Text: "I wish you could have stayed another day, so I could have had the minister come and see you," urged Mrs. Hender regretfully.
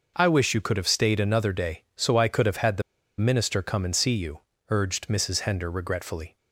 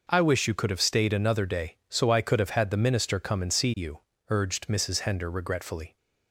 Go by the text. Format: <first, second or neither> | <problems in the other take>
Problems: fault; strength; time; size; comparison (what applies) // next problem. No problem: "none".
second | pauses between "the" and "minister"; at 2.8 s; 0.36 s long